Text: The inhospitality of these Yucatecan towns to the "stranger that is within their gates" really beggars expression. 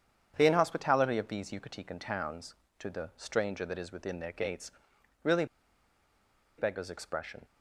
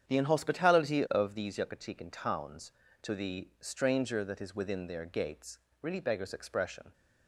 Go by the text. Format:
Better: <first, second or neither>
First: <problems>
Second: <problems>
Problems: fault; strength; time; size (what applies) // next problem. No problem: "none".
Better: second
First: starts louder than the rest; strong; until 1.3 s; 8 dB // pauses between "gates" and "really"; noticeable; at 4.7 s; 0.50 s long // pauses between "really" and "beggars"; at 5.4 s; 1.1 s long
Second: starts louder than the rest; strong; until 1.1 s; 8.5 dB // pauses between "gates" and "really"; slight; at 5.5 s; 0.22 s long